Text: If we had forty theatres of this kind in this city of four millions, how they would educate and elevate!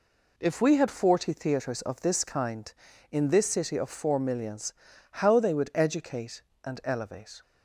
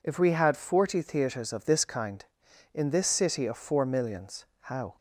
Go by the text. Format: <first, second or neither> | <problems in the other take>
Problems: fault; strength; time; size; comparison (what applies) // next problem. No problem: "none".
first | stops before "they would educate and elevate"; at 4.9 s